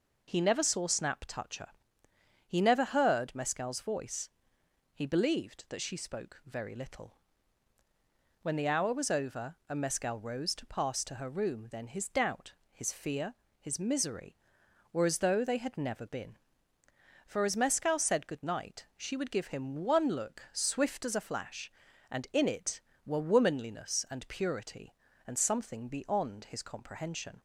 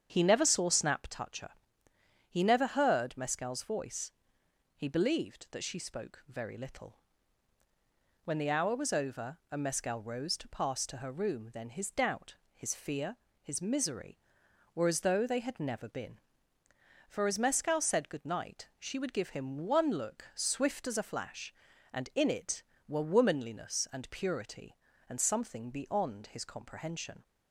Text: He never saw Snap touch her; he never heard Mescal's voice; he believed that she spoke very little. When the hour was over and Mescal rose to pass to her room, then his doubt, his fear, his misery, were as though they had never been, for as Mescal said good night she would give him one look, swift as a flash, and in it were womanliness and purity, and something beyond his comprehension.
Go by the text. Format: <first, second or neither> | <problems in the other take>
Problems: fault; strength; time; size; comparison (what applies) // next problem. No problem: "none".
first | starts louder than the rest; strong; until 1.1 s; 8 dB